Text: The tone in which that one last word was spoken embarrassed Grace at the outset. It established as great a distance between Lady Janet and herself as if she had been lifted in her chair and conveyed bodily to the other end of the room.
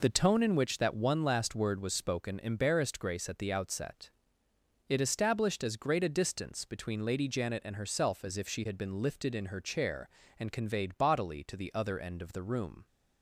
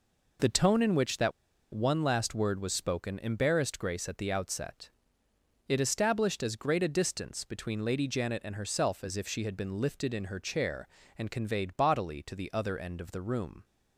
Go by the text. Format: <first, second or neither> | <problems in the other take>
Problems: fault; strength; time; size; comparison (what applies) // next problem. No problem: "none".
first | pauses between "that" and "one"; at 1.3 s; 0.42 s long